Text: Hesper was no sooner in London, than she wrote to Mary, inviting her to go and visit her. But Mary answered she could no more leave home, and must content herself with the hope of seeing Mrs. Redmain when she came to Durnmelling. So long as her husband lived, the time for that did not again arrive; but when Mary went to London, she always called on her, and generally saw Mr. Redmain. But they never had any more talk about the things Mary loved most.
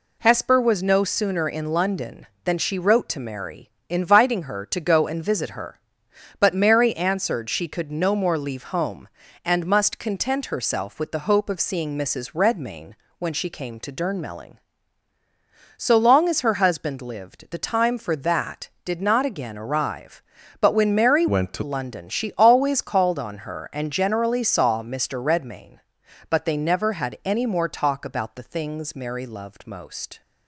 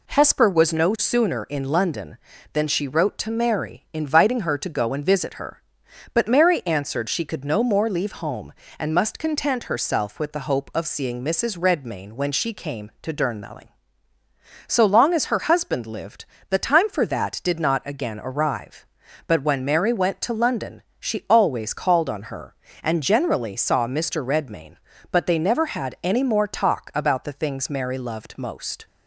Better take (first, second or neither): second